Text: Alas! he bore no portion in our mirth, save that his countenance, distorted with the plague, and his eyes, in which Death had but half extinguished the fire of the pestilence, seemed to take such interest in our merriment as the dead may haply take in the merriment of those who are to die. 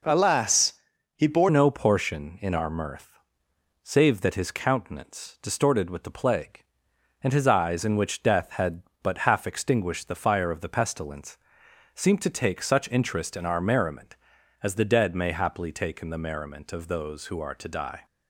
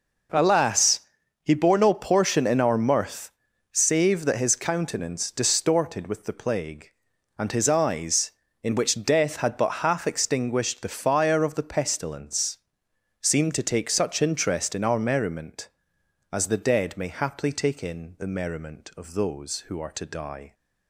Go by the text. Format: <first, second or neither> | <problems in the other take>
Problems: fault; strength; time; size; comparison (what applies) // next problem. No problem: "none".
second | changes voice at "no"; from 1.4 s on; 16.6 s long